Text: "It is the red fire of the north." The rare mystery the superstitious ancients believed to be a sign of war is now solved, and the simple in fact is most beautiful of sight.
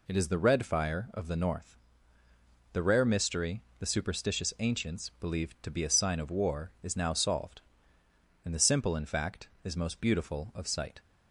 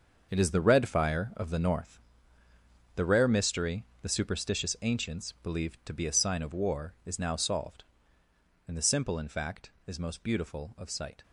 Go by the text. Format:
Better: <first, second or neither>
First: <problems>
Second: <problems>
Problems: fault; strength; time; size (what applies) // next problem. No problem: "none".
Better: first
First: pauses between "mystery" and "the"; slight; at 3.6 s; 0.16 s long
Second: gets quieter; strong; throughout; 11 dB // pauses between "mystery" and "the"; slight; at 3.8 s; 0.16 s long